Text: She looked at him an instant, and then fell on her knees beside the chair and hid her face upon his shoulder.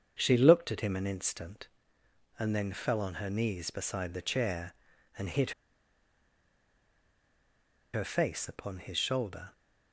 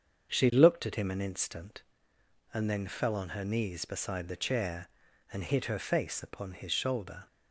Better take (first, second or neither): second